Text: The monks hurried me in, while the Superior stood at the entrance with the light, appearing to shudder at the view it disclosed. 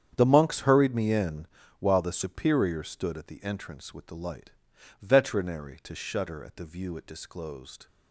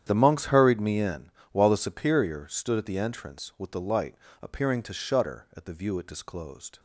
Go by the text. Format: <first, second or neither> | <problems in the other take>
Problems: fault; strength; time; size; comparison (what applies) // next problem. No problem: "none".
second | starts louder than the rest; strong; until 1.1 s; 8.5 dB; strong in the second // says "veterinary" for "appearing"; at 5.0 s